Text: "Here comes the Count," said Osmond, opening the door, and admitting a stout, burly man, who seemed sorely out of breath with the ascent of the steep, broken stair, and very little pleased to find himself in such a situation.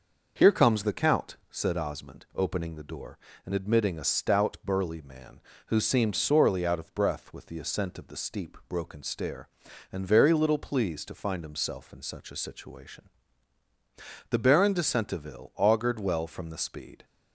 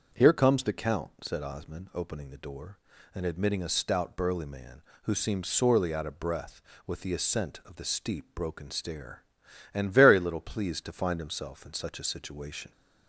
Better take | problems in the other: second | starts louder than the rest; noticeable; until 1.3 s; 6 dB; also in the second // goes on to say "The Baron de Centeville augured well from the speed"; strong; from 14.3 s on; 2.7 s long

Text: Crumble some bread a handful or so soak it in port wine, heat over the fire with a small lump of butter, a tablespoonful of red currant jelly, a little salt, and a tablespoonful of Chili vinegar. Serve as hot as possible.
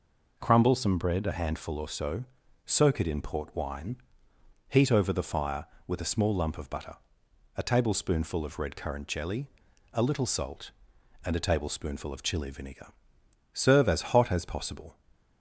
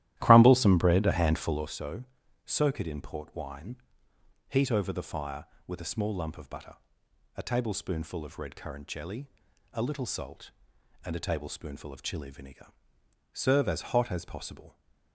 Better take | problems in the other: first | starts louder than the rest; strong; until 1.8 s; 13.5 dB // pauses between "so" and "soak"; noticeable; at 2.0 s; 0.46 s long; noticeable in the first

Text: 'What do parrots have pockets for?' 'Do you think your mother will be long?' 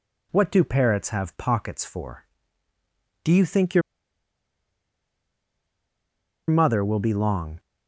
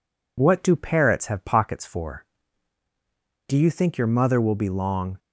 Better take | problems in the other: second | pauses between "your" and "mother"; strong; at 3.8 s; 2.6 s long

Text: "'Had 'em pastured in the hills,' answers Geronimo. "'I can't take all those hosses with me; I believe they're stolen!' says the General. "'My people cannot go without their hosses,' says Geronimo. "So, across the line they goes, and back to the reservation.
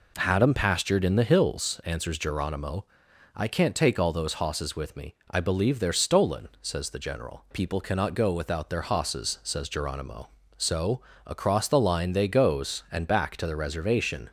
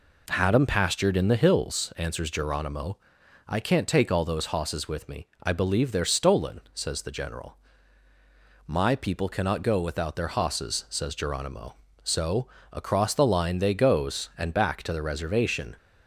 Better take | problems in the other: second | skips "My"; at 7.4 s

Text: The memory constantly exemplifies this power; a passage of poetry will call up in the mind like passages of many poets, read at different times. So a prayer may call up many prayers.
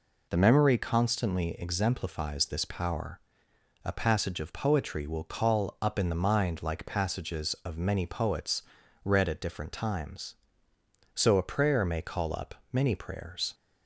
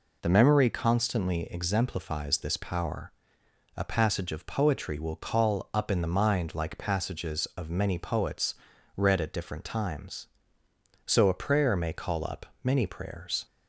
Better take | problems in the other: neither | pauses between "up" and "many"; slight; the same in both

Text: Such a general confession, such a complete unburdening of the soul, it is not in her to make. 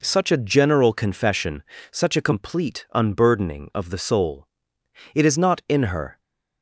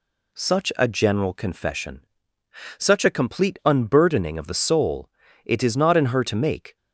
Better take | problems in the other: second | stops before "to make"; at 6.2 s

